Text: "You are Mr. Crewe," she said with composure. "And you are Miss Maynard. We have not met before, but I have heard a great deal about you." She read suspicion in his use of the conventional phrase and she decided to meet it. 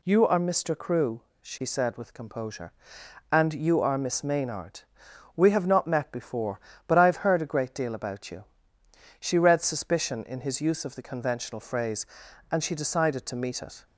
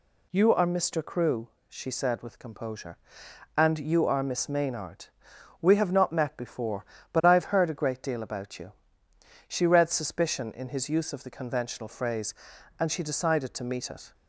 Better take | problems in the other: neither | none

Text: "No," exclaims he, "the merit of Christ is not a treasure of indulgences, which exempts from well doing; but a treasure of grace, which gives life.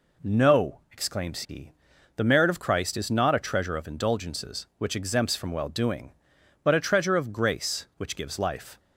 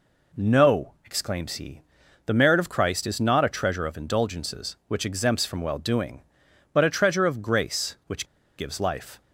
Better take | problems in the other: first | pauses between "which" and "gives"; slight; at 8.2 s; 0.33 s long

